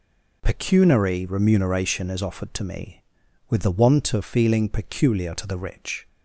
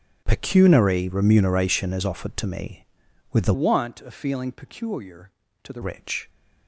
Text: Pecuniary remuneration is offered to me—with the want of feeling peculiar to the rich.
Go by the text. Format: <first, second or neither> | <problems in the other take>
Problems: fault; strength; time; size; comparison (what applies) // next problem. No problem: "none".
first | starts louder than the rest; strong; until 1.2 s; 7.5 dB // changes voice from "want" to "the"; from 3.5 to 5.8 s; 2.3 s long